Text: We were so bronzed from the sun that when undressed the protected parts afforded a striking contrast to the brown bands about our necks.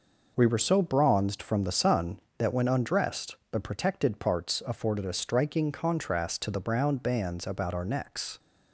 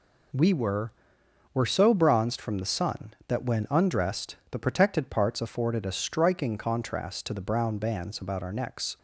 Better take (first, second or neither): first